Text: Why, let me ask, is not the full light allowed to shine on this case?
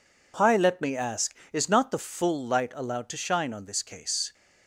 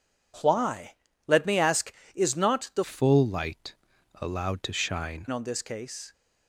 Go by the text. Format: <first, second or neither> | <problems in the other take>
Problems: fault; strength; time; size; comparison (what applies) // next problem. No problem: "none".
first | changes voice from "full" to "shine"; from 2.8 to 5.2 s; 2.4 s long // pauses between "light" and "allowed"; noticeable; at 3.7 s; 0.48 s long